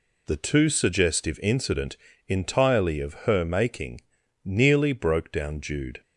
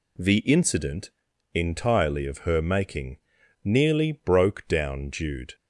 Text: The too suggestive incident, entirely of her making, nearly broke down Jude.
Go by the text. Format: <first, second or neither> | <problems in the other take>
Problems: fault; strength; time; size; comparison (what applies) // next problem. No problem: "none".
first | skips "too suggestive"; at 0.3 s